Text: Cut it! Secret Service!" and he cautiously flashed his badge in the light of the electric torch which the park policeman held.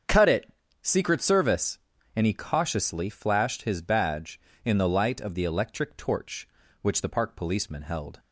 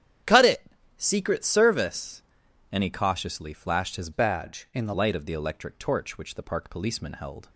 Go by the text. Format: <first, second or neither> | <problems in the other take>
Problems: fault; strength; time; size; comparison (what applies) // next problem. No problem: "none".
first | starts louder than the rest; strong; until 1.6 s; 10 dB; also in the first // changes voice from "badge" to "the"; from 4.1 to 4.9 s; 0.8 s long